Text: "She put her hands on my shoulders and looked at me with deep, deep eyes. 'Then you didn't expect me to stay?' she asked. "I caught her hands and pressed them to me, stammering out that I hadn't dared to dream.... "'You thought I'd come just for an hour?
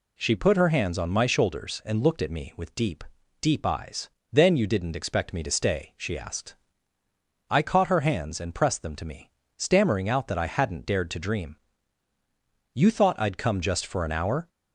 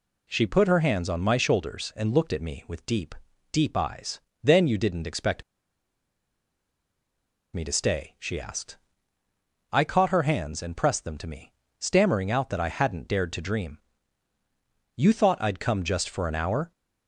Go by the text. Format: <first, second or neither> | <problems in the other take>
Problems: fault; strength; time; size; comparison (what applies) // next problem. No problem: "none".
first | pauses between "expect" and "me"; strong; at 5.4 s; 2.1 s long